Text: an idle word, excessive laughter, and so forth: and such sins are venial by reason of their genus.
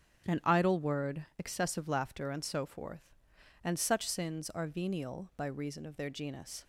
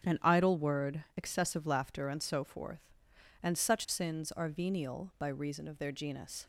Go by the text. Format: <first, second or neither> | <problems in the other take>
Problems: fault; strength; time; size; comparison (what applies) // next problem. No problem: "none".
neither | starts louder than the rest; strong; the same in both